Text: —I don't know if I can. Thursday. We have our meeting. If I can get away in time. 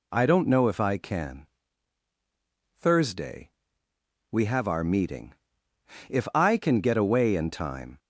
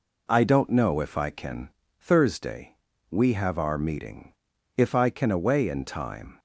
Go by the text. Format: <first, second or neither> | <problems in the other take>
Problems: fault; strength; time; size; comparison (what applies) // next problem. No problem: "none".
first | skips "get"; at 5.3 s